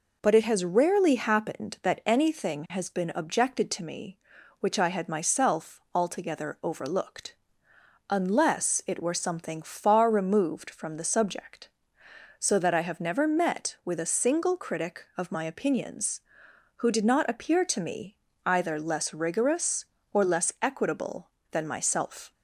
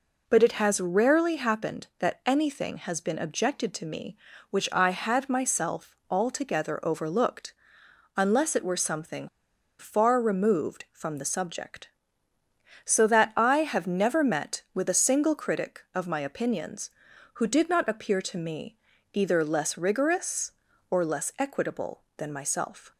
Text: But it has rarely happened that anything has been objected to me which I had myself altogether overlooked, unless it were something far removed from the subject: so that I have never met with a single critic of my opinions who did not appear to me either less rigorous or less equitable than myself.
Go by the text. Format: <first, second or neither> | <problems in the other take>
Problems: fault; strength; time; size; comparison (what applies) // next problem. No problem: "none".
first | pauses between "something" and "far"; noticeable; at 9.2 s; 0.51 s long // pauses between "me" and "either"; at 18.7 s; 0.38 s long; slight in the first